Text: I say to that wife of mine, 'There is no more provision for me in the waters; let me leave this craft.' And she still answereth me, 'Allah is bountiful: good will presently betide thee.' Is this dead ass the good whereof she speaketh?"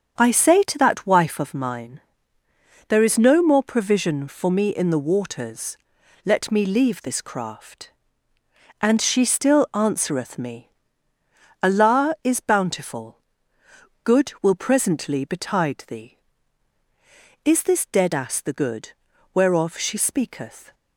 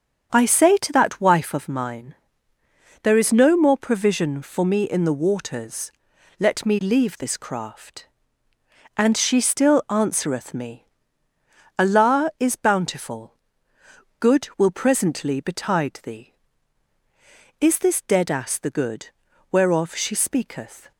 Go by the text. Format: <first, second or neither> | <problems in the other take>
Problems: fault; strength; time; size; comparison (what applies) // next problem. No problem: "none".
neither | starts louder than the rest; strong; the same in both // pauses between "good" and "whereof"; the same in both